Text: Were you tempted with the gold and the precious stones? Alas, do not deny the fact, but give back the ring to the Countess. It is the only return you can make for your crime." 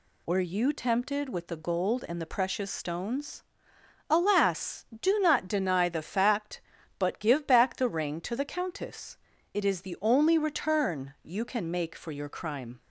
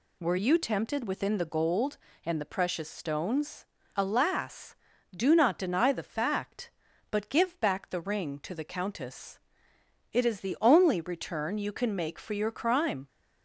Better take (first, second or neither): first